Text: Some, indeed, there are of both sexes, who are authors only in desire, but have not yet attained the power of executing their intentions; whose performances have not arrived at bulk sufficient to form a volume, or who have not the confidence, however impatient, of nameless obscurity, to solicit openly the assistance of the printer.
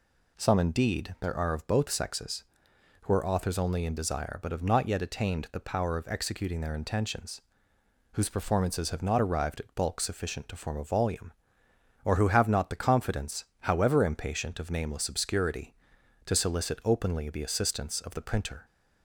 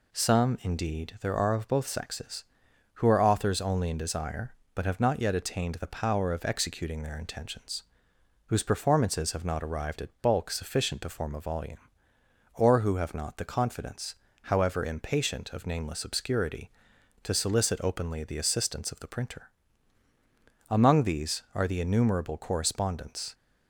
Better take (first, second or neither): first